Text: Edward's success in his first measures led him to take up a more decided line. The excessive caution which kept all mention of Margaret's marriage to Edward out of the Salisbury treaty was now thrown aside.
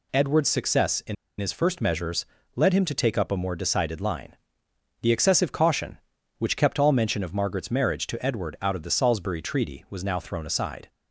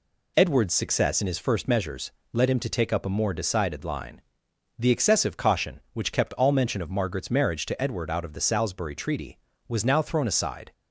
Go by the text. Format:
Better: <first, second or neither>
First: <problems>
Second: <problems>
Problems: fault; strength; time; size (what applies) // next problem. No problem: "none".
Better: second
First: pauses between "in" and "his"; slight; at 1.1 s; 0.25 s long // pauses between "measures" and "led"; slight; at 2.2 s; 0.32 s long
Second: pauses between "measures" and "led"; slight; at 2.0 s; 0.22 s long